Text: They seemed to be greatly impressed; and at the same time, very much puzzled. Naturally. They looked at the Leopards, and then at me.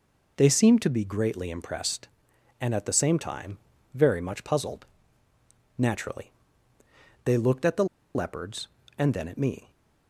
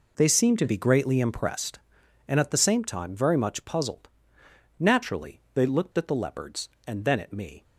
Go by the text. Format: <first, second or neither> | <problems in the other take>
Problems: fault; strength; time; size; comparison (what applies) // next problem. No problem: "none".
second | pauses between "the" and "Leopards"; slight; at 7.8 s; 0.30 s long